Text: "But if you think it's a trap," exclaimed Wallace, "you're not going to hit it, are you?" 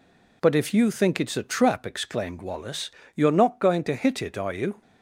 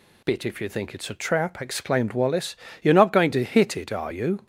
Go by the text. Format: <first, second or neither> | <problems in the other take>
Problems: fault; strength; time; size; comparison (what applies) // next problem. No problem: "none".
first | says "Bit" for "But"; at 0.2 s